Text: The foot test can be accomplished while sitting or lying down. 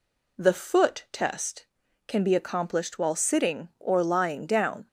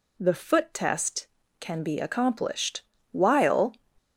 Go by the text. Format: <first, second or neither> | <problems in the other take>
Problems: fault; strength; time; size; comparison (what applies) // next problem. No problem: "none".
first | pauses between "accomplished" and "while"; slight; at 2.8 s; 0.28 s long // stops before "sitting or lying down"; at 3.9 s